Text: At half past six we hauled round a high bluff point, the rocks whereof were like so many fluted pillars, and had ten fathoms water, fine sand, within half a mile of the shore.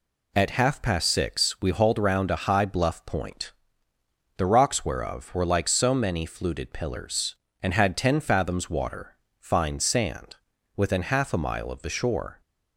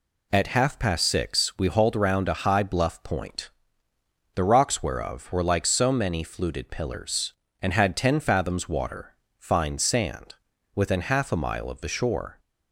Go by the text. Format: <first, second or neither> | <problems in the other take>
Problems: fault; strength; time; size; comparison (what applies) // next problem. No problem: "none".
neither | none